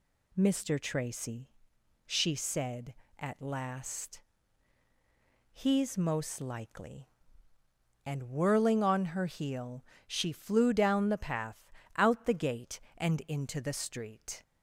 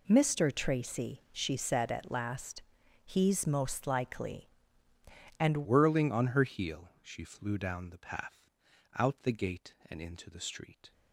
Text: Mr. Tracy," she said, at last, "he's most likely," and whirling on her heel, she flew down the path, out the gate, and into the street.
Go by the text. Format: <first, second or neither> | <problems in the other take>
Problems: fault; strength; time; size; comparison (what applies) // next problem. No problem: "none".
first | changes voice at "whirling"; from 5.6 s on; 5.3 s long